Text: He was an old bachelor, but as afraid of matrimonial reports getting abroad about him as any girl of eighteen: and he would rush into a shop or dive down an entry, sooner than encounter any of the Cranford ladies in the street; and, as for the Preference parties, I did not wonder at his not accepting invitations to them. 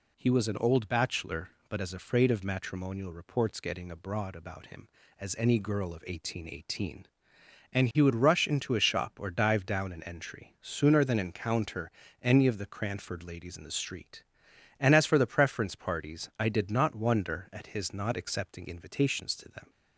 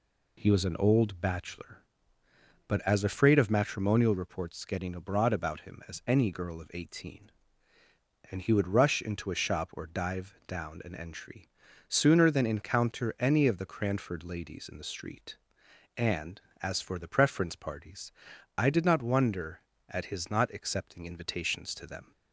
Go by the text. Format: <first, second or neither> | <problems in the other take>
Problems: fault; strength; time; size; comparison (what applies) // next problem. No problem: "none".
second | says "eighteen" twice; at 6.4 s // pauses between "encounter" and "any"; slight; at 11.9 s; 0.30 s long